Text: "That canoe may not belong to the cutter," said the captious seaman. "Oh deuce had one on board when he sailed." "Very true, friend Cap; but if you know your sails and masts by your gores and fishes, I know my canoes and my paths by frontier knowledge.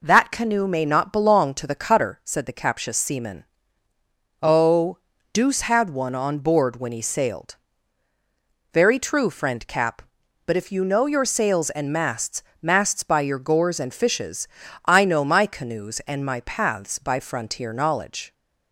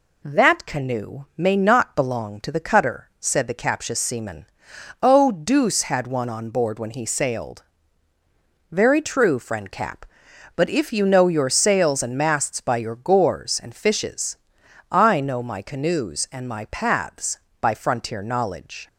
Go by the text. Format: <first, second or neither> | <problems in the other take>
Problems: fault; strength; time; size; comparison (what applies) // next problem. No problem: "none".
second | pauses between "Oh" and "deuce"; slight; at 4.9 s; 0.34 s long // says "masts" twice; at 12.6 s